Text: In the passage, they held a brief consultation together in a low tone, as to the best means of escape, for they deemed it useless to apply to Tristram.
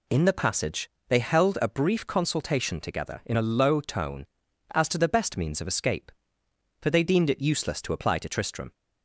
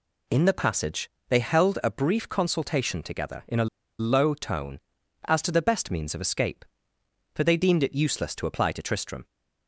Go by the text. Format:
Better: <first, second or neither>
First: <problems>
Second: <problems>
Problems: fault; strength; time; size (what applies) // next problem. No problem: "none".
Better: first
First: none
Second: pauses between "a" and "low"; slight; at 3.6 s; 0.33 s long